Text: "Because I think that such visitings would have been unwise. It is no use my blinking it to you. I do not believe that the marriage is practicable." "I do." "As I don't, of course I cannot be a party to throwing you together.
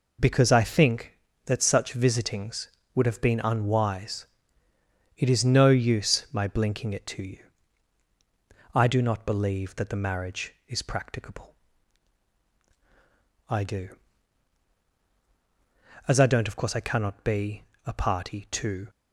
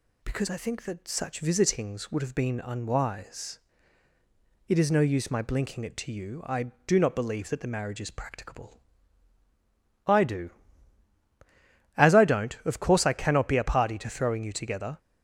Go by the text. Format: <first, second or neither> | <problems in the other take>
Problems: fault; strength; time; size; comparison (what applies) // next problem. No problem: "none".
second | pauses between "be" and "a"; slight; at 17.6 s; 0.22 s long // stops before "throwing you together"; at 18.8 s